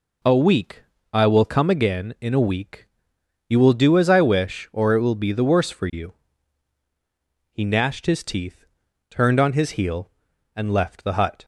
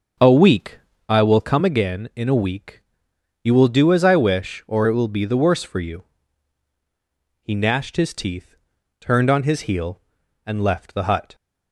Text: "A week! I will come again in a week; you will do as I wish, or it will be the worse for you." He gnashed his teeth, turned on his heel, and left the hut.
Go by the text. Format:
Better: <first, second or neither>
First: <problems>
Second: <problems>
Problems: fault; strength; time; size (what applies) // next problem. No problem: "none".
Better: first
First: none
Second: starts louder than the rest; until 1.2 s; 6.5 dB